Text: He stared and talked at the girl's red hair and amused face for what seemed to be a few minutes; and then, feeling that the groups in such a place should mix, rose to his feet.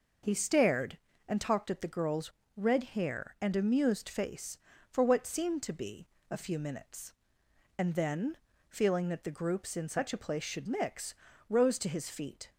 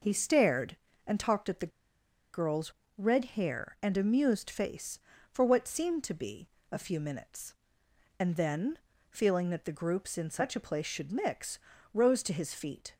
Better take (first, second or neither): first